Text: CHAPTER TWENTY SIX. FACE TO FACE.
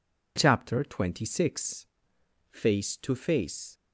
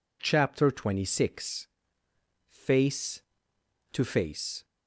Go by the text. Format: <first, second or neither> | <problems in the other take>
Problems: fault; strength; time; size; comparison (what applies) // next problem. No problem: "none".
neither | none